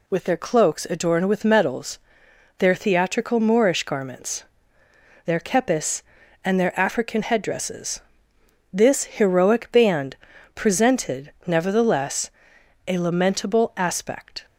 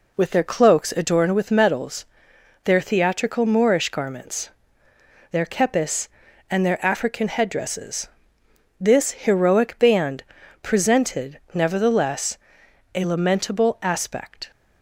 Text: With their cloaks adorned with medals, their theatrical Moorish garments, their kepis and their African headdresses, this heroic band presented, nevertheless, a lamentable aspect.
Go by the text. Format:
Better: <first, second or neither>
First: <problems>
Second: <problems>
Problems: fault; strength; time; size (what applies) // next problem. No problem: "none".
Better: first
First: pauses between "band" and "presented"; at 10.1 s; 0.40 s long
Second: starts louder than the rest; slight; until 1.4 s; 3 dB // pauses between "band" and "presented"; at 10.2 s; 0.40 s long